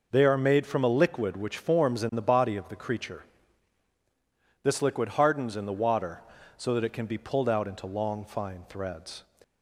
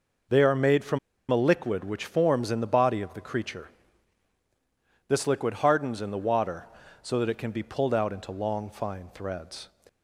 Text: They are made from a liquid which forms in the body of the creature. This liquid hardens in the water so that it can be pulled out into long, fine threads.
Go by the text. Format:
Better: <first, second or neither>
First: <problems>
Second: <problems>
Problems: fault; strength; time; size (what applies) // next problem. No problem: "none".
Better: first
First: none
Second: pauses between "from" and "a"; slight; at 0.9 s; 0.32 s long